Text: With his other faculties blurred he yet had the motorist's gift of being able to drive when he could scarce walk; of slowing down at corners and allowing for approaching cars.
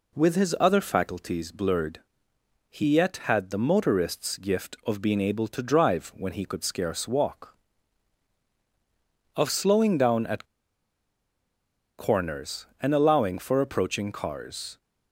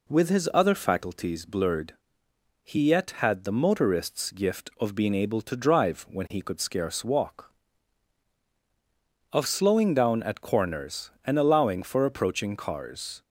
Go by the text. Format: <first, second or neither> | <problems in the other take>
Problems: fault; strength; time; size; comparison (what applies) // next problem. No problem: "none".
second | pauses between "blurred" and "he"; noticeable; at 1.9 s; 0.70 s long; noticeable in the second // pauses between "at" and "corners"; strong; at 10.4 s; 1.5 s long